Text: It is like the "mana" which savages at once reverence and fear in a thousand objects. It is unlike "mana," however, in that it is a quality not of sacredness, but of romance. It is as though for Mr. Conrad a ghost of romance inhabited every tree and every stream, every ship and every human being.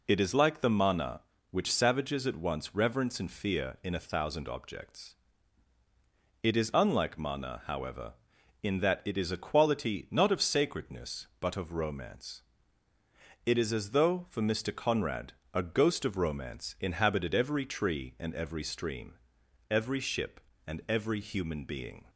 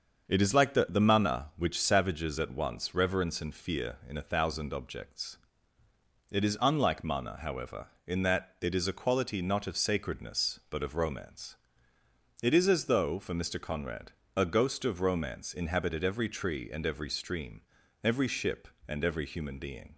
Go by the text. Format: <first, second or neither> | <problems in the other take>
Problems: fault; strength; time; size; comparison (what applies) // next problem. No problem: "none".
first | starts louder than the rest; until 1.3 s; 6.5 dB // says "the" twice; at 0.8 s // pauses between "Conrad" and "a"; slight; at 14.1 s; 0.24 s long; slight in the first